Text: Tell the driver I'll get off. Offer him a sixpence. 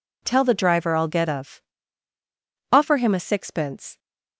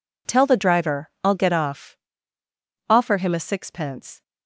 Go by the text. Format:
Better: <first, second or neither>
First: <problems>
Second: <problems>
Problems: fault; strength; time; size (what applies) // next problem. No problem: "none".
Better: second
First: says "of" for "off"; at 1.2 s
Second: none